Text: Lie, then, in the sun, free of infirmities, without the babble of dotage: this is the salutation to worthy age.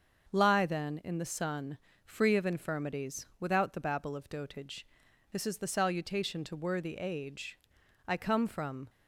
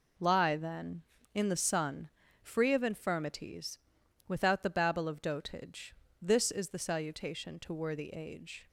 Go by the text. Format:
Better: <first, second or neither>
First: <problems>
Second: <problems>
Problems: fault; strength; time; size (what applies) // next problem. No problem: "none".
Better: second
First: starts louder than the rest; until 1.3 s; 6.5 dB // goes on to say "I come from"; noticeable; from 8.0 s on; 0.84 s long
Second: none